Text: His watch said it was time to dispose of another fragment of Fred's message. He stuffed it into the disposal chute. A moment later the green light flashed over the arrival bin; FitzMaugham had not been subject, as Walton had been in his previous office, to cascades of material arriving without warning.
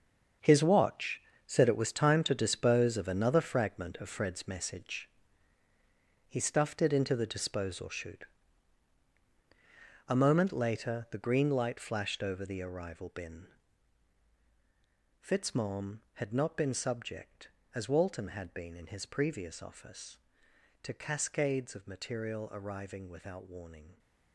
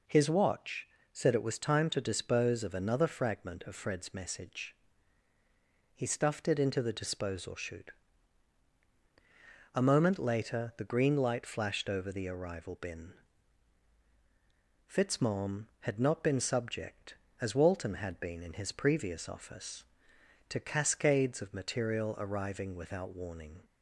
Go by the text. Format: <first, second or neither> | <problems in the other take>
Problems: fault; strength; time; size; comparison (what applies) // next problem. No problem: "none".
second | gets quieter; strong; throughout; 11.5 dB // pauses between "watch" and "said"; slight; at 1.2 s; 0.26 s long; slight in the second